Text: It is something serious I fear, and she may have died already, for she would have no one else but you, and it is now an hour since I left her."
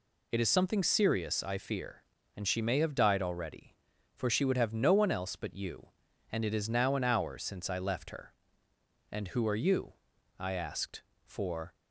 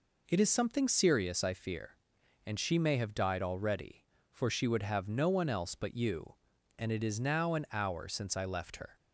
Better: second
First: goes on to say "And who are you I asked for"; strong; from 9.0 s on; 2.6 s long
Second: none

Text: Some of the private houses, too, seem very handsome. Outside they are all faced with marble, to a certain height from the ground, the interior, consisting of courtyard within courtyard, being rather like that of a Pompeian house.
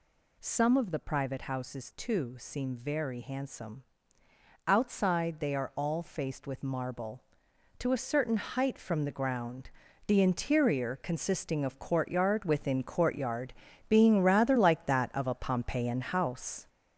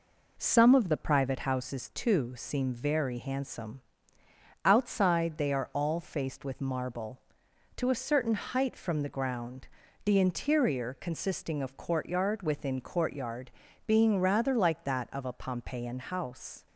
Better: second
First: gets louder; noticeable; throughout; 6 dB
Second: none

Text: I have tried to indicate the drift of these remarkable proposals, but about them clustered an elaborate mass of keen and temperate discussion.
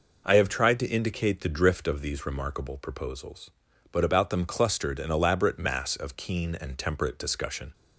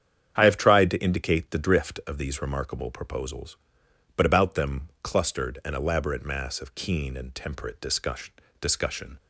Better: first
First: none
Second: starts louder than the rest; strong; until 1.3 s; 8.5 dB // says "discussion" twice; at 8.5 s

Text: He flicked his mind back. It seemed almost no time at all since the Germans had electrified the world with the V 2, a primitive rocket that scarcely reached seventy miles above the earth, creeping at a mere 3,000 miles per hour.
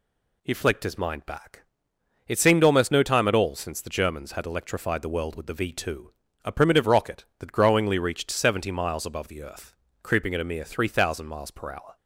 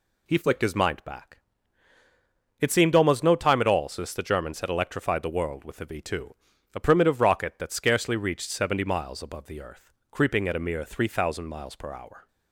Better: second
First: says "growingly" for "scarcely"; at 7.5 s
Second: none

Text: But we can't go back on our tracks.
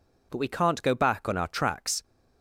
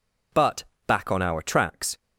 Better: first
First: none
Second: skips "we can't go"; at 0.7 s

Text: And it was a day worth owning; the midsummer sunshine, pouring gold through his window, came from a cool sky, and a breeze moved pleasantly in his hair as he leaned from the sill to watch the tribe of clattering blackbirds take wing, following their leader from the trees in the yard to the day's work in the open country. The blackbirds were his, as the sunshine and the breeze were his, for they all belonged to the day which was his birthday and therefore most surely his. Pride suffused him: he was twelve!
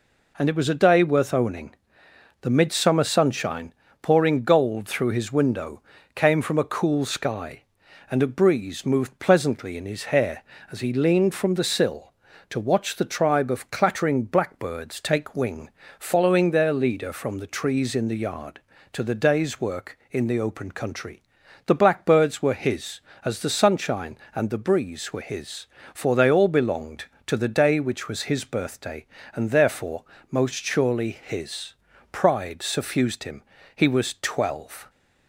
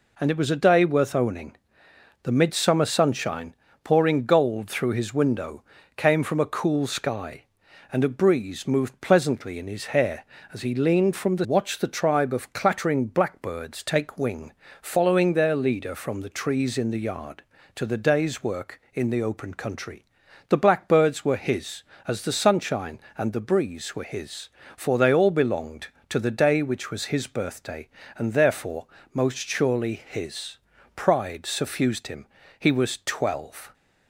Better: first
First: pauses between "therefore" and "most"; slight; at 30.0 s; 0.26 s long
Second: skips "sill to"; at 11.4 s // pauses between "therefore" and "most"; slight; at 28.8 s; 0.26 s long

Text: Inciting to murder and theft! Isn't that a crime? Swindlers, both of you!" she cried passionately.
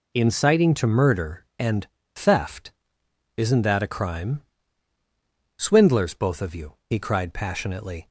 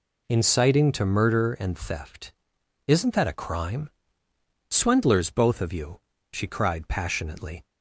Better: second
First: pauses between "and" and "theft"; slight; at 1.8 s; 0.28 s long // says "he" for "she"; at 6.8 s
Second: none

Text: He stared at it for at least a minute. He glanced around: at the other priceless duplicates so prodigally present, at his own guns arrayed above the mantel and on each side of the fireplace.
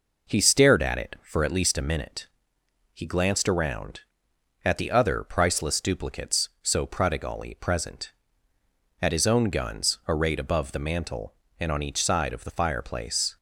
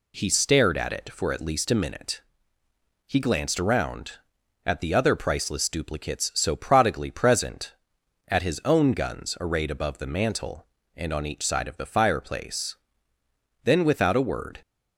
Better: first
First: none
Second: goes on to say "Then without a word"; noticeable; from 13.6 s on; 0.96 s long

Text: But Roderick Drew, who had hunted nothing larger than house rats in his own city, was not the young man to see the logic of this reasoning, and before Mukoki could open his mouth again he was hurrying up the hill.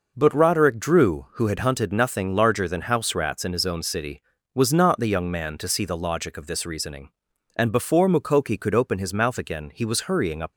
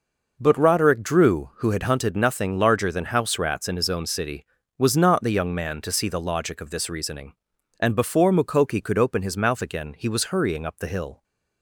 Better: second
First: stops before "the hill"; at 10.5 s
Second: none

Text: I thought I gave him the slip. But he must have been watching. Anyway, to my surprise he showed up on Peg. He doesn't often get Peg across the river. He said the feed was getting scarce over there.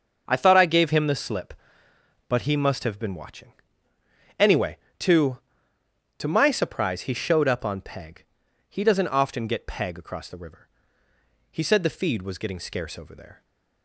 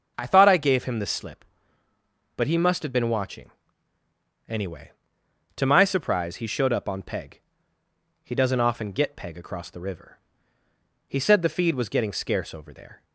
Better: second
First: starts louder than the rest; until 1.2 s; 6.5 dB // says "to" twice; at 6.1 s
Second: starts louder than the rest; until 1.1 s; 6.5 dB

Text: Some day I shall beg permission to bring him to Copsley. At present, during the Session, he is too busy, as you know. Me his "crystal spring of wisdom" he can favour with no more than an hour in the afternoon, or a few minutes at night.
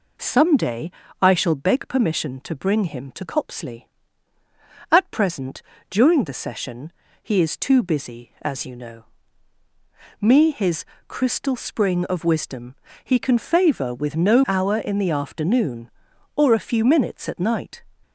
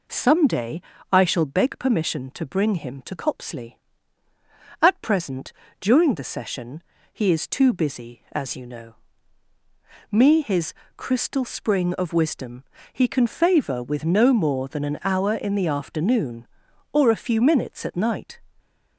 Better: second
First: pauses between "day" and "I"; slight; at 0.8 s; 0.32 s long // pauses between "his" and "crystal"; slight; at 10.8 s; 0.24 s long // pauses between "wisdom" and "he"; slight; at 12.7 s; 0.30 s long // skips "more than an"; at 14.4 s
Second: pauses between "day" and "I"; slight; at 0.7 s; 0.32 s long // pauses between "his" and "crystal"; slight; at 10.7 s; 0.24 s long // pauses between "wisdom" and "he"; slight; at 12.6 s; 0.30 s long

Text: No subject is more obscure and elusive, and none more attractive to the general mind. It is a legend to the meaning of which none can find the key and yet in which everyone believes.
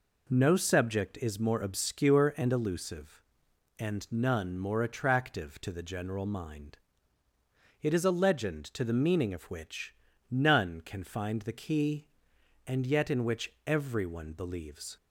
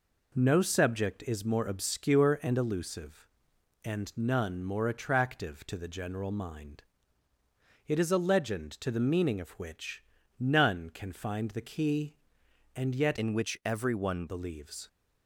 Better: first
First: pauses between "which" and "none"; slight; at 9.9 s; 0.36 s long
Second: pauses between "which" and "none"; slight; at 10.0 s; 0.36 s long // changes voice from "in" to "everyone"; from 13.1 to 14.2 s; 1.1 s long

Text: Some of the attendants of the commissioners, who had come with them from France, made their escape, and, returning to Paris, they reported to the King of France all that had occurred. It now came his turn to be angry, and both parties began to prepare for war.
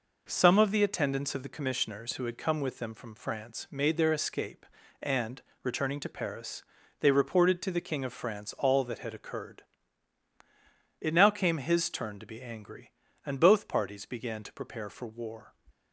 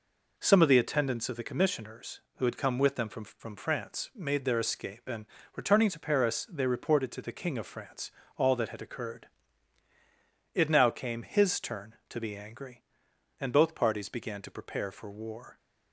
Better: first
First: none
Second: says "from" twice; at 3.2 s // pauses between "France" and "all"; slight; at 8.1 s; 0.26 s long

